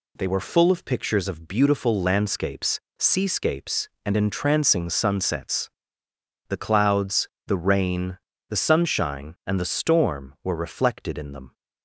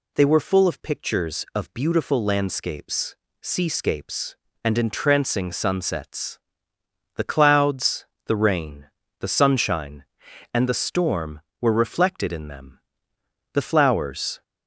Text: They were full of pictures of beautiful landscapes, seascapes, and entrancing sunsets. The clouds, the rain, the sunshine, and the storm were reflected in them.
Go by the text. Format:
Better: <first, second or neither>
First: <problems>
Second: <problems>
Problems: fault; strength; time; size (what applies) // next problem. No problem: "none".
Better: first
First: none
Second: goes on to say "The flowers"; noticeable; from 13.5 s on; 0.88 s long